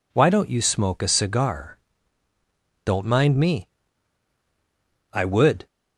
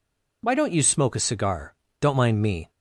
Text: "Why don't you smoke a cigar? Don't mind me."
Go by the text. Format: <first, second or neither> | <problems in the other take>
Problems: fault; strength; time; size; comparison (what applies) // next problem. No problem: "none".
second | goes on to say "I would"; from 5.1 s on; 0.54 s long